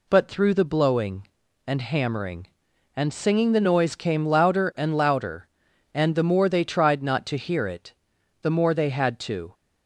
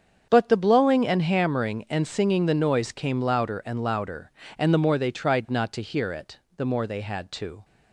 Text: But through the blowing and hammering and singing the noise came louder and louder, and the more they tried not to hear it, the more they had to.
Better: first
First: none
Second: starts louder than the rest; strong; until 1.3 s; 7 dB // skips "through"; at 0.5 s

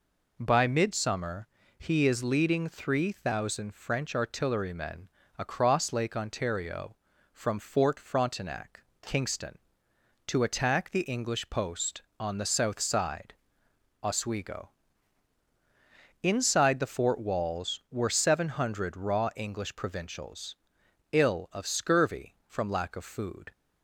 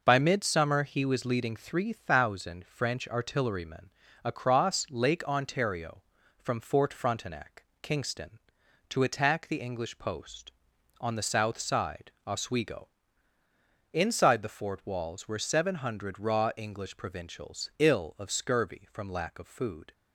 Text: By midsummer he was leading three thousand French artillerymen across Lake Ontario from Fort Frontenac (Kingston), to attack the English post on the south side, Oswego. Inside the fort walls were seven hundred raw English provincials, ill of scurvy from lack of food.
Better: second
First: pauses between "midsummer" and "he"; slight; at 1.4 s; 0.30 s long // says "is" for "was"; at 2.0 s // pauses between "artillerymen" and "across"; slight; at 5.0 s; 0.28 s long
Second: pauses between "artillerymen" and "across"; slight; at 3.8 s; 0.34 s long

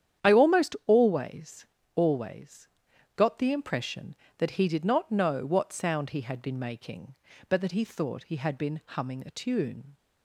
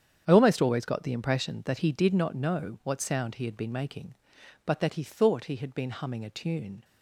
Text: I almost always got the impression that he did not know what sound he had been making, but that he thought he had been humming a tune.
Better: second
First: starts louder than the rest; strong; until 1.3 s; 9.5 dB // says "always" twice; at 1.9 s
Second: starts louder than the rest; strong; until 1.2 s; 8.5 dB

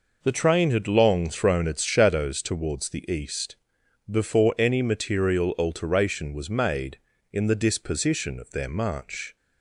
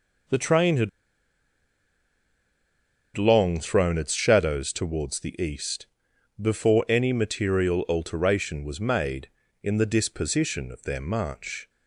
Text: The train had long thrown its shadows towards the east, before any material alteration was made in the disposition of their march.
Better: first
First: none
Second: pauses between "had" and "long"; strong; at 0.8 s; 2.2 s long

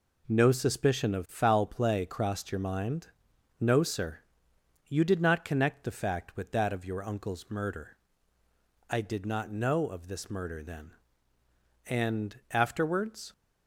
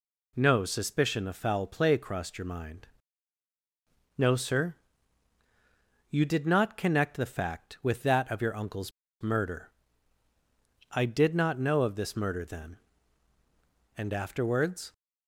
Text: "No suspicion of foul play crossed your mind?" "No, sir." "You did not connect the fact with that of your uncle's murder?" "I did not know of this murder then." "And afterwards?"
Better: first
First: none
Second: pauses between "uncle's" and "murder"; slight; at 8.9 s; 0.31 s long

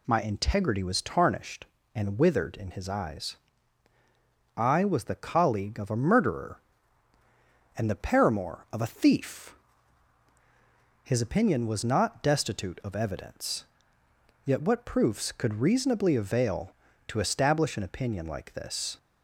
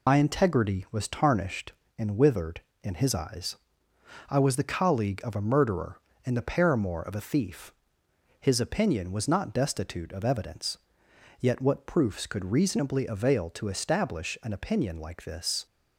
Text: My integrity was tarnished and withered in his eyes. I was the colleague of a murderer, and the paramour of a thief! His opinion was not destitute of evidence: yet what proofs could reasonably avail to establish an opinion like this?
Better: first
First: none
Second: loses the start of "My"; at 0.0 s; 70 ms

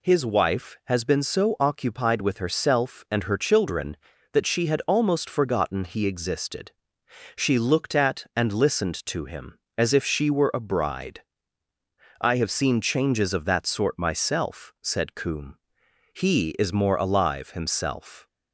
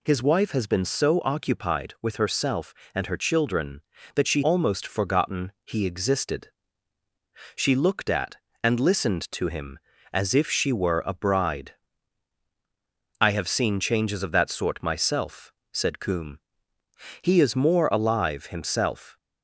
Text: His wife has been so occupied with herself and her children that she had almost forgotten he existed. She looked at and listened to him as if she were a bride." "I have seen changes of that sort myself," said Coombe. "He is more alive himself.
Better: first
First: none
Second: skips "had"; at 4.4 s

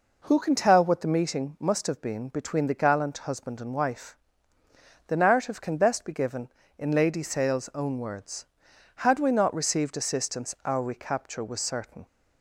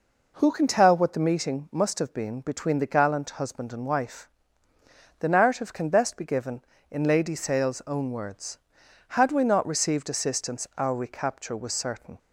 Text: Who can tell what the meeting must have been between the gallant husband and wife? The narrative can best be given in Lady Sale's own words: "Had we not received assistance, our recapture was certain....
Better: neither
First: none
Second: none

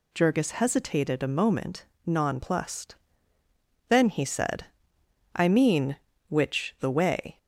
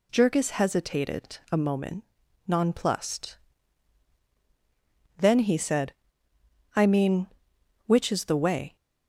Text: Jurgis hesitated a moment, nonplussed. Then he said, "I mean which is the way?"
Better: second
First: skips "is"; at 6.7 s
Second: none

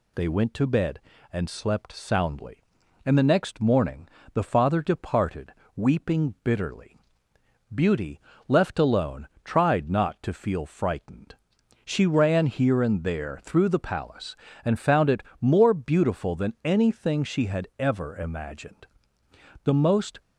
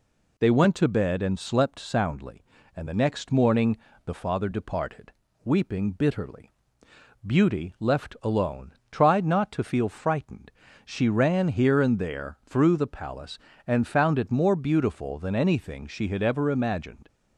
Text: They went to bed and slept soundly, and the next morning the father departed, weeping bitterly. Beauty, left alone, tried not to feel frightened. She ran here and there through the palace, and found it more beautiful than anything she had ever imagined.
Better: second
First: pauses between "morning" and "the"; slight; at 4.0 s; 0.24 s long // pauses between "it" and "more"; slight; at 15.2 s; 0.20 s long // goes on to say "The most"; from 19.6 s on; 0.56 s long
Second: pauses between "morning" and "the"; slight; at 3.7 s; 0.26 s long

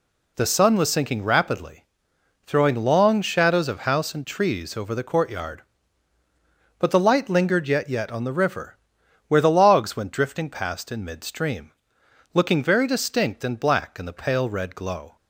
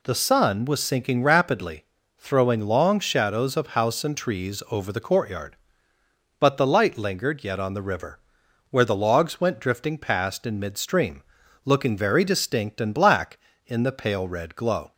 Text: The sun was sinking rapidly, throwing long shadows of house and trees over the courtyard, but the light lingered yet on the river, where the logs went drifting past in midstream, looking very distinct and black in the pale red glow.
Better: second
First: says "yet" twice; at 7.8 s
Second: none

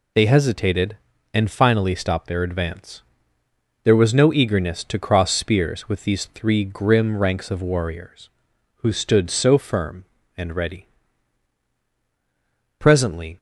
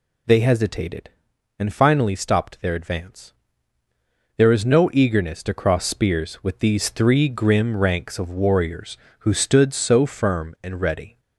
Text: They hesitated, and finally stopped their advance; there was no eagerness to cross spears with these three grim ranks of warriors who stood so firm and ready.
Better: second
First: goes on to say "Presently"; from 12.7 s on; 0.58 s long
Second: none

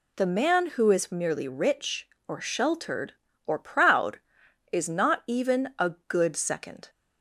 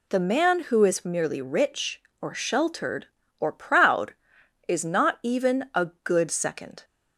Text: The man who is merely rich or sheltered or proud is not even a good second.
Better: neither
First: none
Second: none

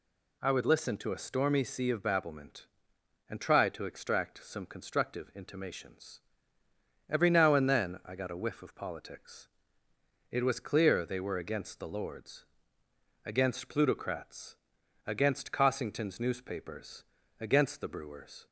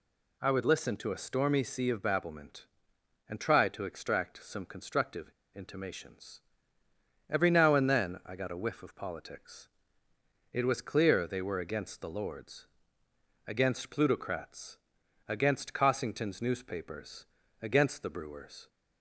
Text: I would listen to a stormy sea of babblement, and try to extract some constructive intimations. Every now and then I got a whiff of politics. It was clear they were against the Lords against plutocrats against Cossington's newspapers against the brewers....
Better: first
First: pauses between "Lords" and "against"; noticeable; at 12.4 s; 0.80 s long // pauses between "plutocrats" and "against"; noticeable; at 14.5 s; 0.50 s long // pauses between "newspapers" and "against"; at 17.0 s; 0.38 s long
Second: pauses between "constructive" and "intimations"; slight; at 5.3 s; 0.22 s long // pauses between "Lords" and "against"; noticeable; at 12.6 s; 0.80 s long // pauses between "plutocrats" and "against"; noticeable; at 14.7 s; 0.50 s long // pauses between "newspapers" and "against"; at 17.2 s; 0.38 s long

